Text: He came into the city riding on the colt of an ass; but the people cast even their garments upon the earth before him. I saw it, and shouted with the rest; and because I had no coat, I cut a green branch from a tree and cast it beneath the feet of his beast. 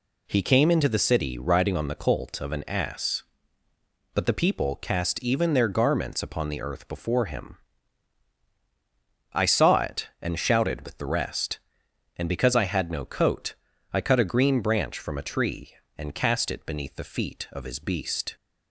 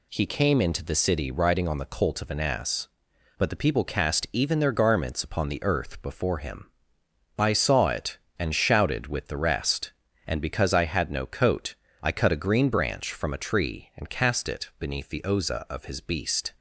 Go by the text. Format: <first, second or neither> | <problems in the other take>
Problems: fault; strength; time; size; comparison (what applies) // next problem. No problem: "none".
first | says "oza" for "feet"; at 15.2 s